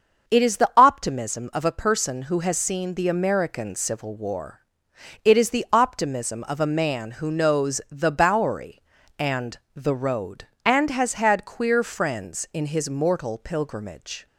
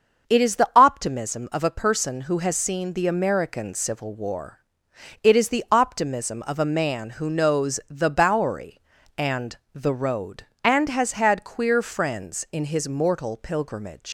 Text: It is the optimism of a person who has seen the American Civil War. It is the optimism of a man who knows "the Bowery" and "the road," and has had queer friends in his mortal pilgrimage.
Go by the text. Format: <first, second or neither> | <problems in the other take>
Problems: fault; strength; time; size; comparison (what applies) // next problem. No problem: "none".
first | starts louder than the rest; until 1.3 s; 6.5 dB; also in the first // pauses between "and" and "the"; slight; at 9.5 s; 0.20 s long; slight in the first // leaves "pilgrimage" unfinished; at 14.0 s; 125 ms